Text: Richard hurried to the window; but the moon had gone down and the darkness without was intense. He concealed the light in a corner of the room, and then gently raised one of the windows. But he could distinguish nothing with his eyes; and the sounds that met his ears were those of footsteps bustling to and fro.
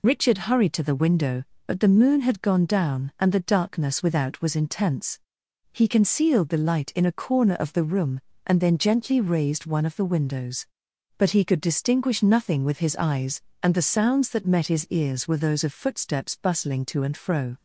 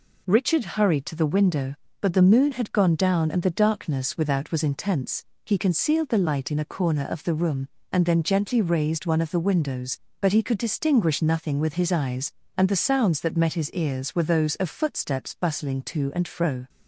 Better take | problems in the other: second | loses the start of "Richard"; at 0.0 s; 40 ms

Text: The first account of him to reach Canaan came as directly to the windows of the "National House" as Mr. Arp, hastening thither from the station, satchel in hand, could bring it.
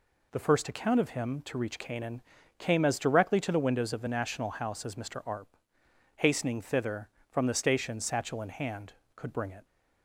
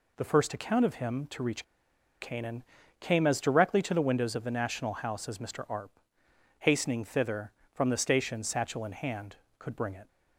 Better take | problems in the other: first | pauses between "reach" and "Canaan"; noticeable; at 1.6 s; 0.56 s long // pauses between "Canaan" and "came"; at 2.6 s; 0.38 s long; also in the first

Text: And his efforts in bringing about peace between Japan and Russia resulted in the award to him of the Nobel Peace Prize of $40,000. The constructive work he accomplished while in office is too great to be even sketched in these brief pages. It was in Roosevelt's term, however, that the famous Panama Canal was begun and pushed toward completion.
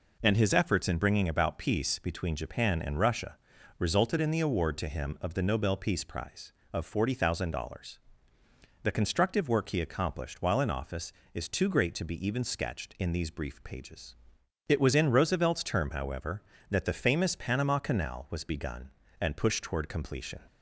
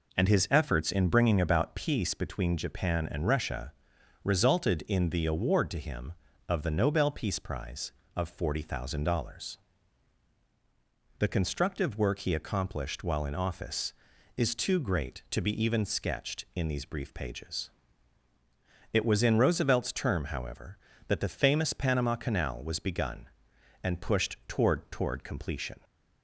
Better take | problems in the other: first | pauses between "Russia" and "resulted"; noticeable; at 3.7 s; 0.52 s long; also in the first // says "toward" twice; at 24.9 s

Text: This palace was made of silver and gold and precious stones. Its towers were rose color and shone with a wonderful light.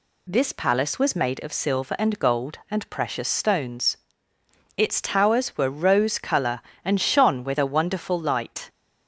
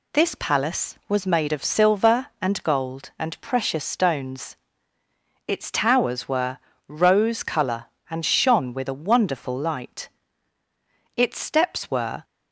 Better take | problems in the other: first | pauses between "were" and "rose"; slight; at 6.5 s; 0.32 s long // goes on to say "Its steps were"; noticeable; from 11.1 s on; 1.0 s long

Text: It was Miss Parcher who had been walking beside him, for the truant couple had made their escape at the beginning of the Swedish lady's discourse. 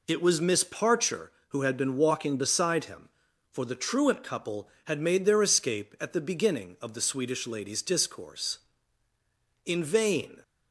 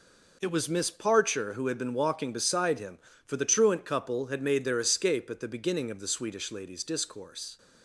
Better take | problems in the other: second | goes on to say "In vain"; noticeable; from 9.6 s on; 0.78 s long

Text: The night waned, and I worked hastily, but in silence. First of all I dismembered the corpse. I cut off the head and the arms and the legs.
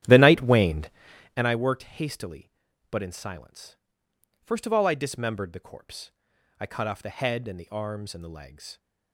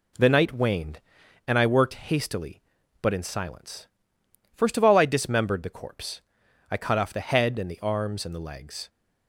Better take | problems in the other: second | starts louder than the rest; strong; until 1.6 s; 11.5 dB

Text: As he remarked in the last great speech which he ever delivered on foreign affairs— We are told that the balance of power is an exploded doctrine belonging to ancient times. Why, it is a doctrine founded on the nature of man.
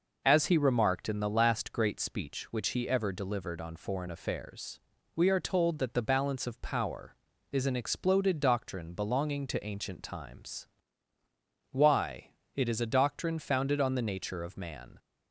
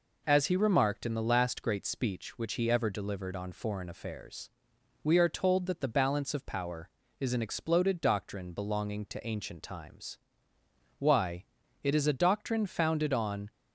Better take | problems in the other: first | stops before "the nature of man"; at 13.5 s

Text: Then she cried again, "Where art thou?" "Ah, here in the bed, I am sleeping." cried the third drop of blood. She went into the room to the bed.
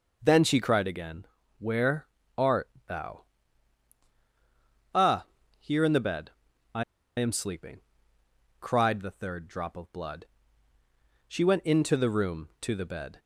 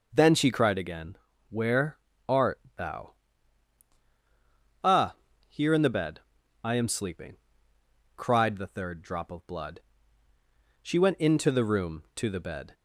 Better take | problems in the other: second | pauses between "Where" and "art"; slight; at 2.0 s; 0.30 s long; slight in the second // pauses between "art" and "thou"; slight; at 2.6 s; 0.18 s long; slight in the second // pauses between "I" and "am"; slight; at 6.8 s; 0.35 s long

